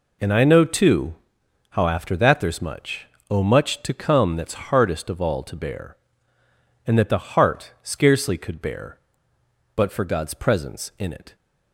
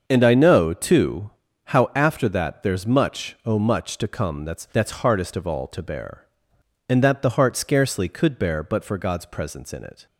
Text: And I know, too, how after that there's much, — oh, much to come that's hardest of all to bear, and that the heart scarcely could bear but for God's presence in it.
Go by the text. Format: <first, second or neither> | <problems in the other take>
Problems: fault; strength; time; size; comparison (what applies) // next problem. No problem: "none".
first | starts louder than the rest; until 1.0 s; 6.5 dB // says "that's" twice; at 4.6 s